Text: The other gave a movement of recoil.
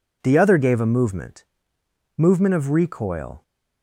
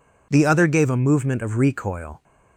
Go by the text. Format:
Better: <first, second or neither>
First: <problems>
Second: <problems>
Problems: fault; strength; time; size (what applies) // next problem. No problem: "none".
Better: second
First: says "movement" twice; at 2.1 s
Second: none